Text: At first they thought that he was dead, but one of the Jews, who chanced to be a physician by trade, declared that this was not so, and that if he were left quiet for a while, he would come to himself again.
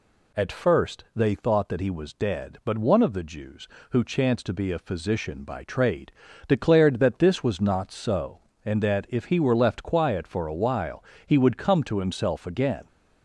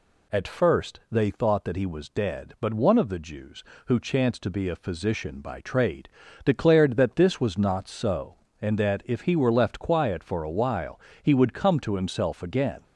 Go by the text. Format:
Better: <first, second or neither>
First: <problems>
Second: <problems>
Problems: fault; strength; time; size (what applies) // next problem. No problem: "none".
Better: neither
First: none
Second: none